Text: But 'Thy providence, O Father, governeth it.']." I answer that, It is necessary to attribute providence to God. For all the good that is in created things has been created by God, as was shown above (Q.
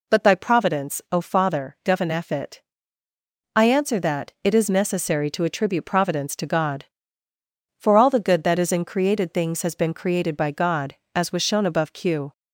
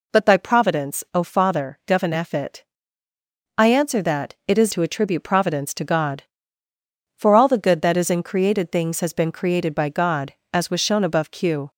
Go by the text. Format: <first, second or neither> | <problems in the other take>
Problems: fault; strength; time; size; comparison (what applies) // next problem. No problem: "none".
first | skips "necessary"; at 4.7 s